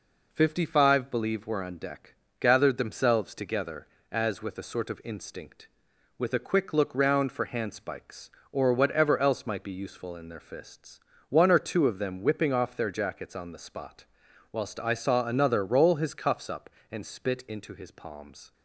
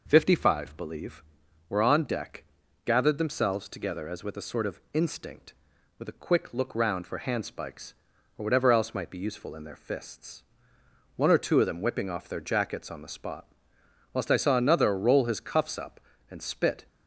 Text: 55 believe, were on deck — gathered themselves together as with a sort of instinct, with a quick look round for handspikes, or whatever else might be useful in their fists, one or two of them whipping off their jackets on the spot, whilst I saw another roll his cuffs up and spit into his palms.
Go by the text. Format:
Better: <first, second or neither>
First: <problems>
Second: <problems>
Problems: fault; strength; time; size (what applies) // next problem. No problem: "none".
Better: first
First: none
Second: stops before "into his palms"; at 16.8 s